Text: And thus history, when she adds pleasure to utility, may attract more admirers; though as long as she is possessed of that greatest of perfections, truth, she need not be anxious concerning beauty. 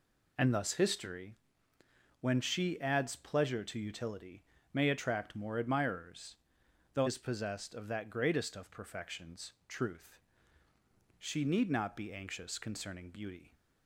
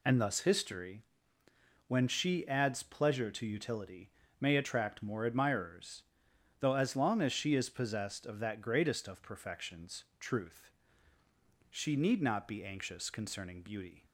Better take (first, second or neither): second